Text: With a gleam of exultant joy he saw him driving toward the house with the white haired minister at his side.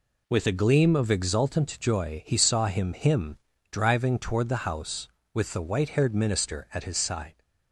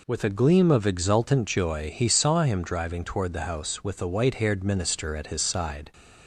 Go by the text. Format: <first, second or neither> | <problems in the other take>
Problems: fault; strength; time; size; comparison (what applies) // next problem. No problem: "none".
second | says "him" twice; at 2.9 s